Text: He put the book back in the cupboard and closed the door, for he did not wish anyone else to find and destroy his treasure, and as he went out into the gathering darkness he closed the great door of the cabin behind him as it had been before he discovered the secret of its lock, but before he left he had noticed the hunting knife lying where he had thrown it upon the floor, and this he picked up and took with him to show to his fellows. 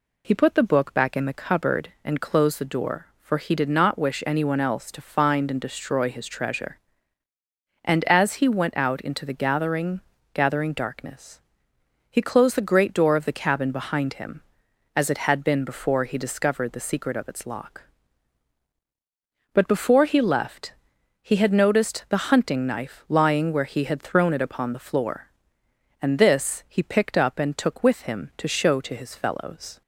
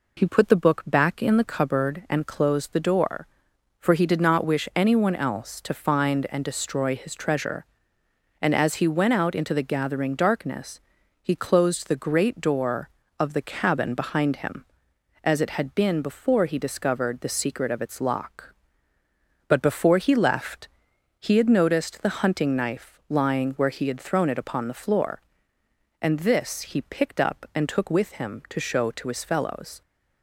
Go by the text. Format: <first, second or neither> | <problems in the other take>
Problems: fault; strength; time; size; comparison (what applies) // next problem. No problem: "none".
second | says "gathering" twice; at 10.3 s // pauses between "darkness" and "he"; noticeable; at 11.3 s; 0.70 s long; also in the second // pauses between "left" and "he"; noticeable; at 20.7 s; 0.48 s long; noticeable in the second